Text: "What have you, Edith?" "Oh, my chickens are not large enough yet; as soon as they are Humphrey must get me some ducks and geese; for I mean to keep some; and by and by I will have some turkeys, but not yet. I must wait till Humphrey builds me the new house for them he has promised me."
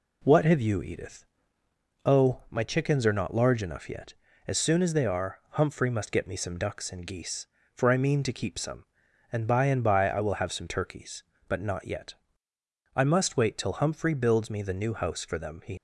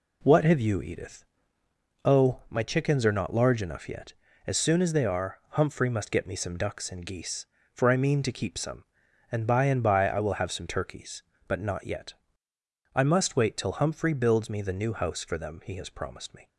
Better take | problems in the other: second | stops before "has promised me"; at 15.7 s

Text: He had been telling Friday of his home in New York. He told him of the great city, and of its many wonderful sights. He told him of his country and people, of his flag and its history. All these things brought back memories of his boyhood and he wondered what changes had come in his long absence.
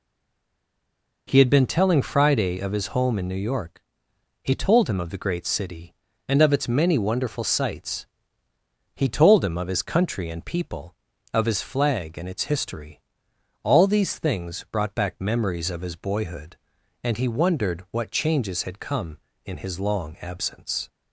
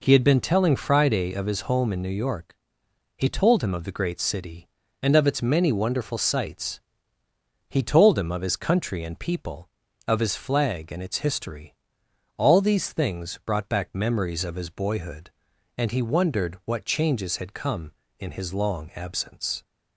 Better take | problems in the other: second | stays silent before the first word; noticeable; until 1.2 s; 1.2 s long

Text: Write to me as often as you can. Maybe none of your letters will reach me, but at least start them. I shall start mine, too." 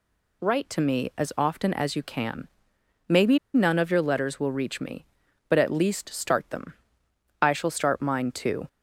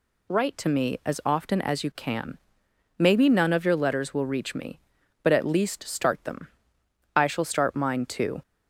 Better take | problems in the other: second | pauses between "Maybe" and "none"; slight; at 3.3 s; 0.17 s long

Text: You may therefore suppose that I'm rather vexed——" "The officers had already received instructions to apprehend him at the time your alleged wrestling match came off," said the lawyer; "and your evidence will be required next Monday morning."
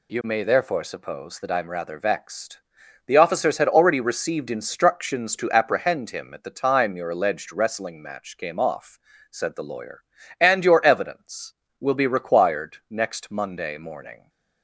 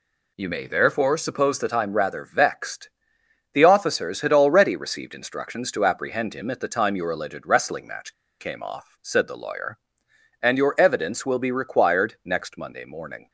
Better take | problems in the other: first | pauses between "match" and "came"; slight; at 8.1 s; 0.26 s long

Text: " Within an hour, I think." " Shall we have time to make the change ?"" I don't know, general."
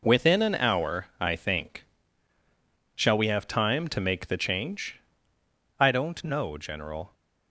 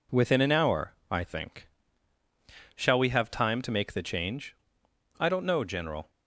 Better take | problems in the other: neither | none

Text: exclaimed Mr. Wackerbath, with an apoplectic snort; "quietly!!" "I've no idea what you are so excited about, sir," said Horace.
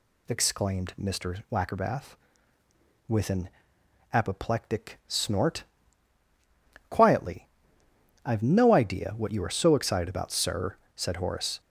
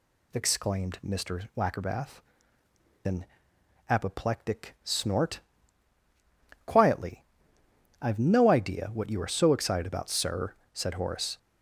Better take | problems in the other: first | skips "with"; at 2.6 s // pauses between "an" and "apoplectic"; noticeable; at 3.2 s; 0.62 s long; noticeable in the first

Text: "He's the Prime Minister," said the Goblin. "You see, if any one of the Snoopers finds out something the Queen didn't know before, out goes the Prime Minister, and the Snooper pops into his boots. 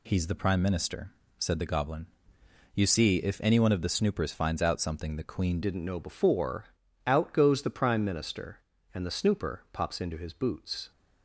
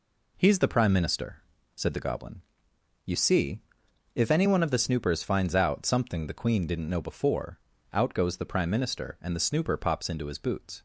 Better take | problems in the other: second | changes voice at "didn't"; from 5.6 s on; 5.3 s long

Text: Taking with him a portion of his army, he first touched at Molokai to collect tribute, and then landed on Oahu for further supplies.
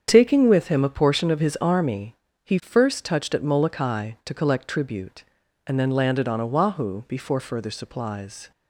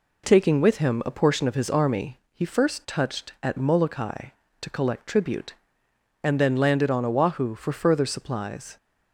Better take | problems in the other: second | starts louder than the rest; strong; until 1.1 s; 7.5 dB // says "before" for "for"; at 7.0 s

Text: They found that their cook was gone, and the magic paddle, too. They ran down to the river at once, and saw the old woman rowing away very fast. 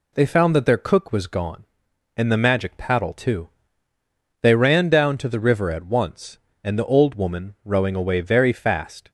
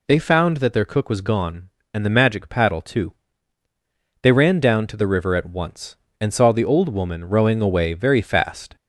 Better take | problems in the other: second | skips "saw"; at 6.7 s

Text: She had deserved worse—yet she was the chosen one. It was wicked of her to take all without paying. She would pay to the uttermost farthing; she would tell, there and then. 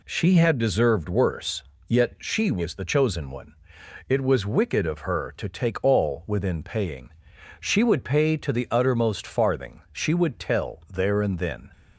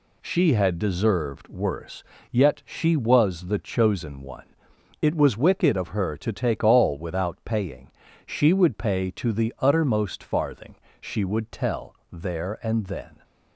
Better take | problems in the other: second | says "within" for "without"; at 6.2 s

